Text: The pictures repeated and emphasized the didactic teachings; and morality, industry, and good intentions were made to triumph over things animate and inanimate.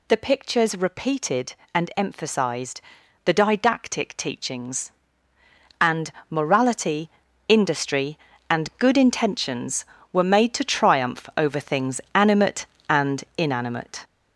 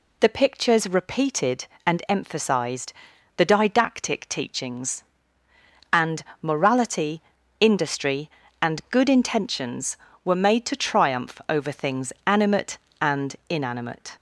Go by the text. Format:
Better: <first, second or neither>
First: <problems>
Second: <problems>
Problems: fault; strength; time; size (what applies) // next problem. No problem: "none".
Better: second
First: gets louder; noticeable; throughout; 5 dB // pauses between "emphasized" and "the"; at 2.8 s; 0.42 s long // pauses between "and" and "morality"; slight; at 6.1 s; 0.16 s long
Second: pauses between "emphasized" and "the"; at 2.9 s; 0.42 s long // pauses between "and" and "morality"; slight; at 6.2 s; 0.16 s long